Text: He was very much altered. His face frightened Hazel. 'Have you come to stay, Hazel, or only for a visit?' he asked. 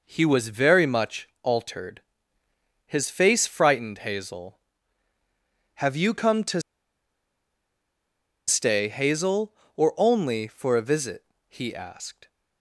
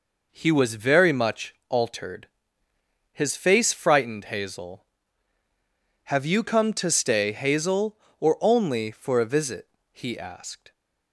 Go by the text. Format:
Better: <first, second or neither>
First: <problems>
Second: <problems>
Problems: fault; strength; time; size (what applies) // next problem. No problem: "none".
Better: second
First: pauses between "to" and "stay"; strong; at 6.6 s; 1.8 s long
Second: none